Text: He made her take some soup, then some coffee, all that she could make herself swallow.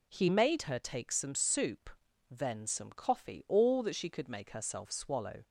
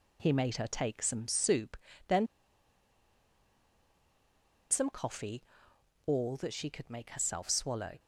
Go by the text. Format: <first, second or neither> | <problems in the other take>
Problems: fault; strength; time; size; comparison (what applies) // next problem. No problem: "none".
first | pauses between "then" and "some"; strong; at 2.2 s; 2.4 s long